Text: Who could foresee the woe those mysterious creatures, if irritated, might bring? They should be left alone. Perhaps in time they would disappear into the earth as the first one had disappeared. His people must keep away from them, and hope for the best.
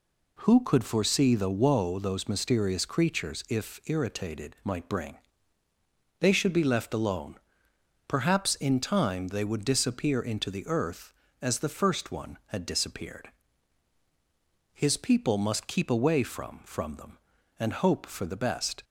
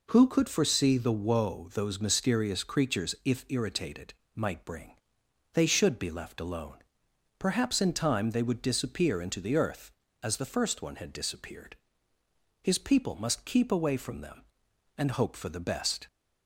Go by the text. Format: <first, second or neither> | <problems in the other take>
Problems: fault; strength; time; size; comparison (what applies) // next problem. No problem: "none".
second | says "from" twice; at 16.6 s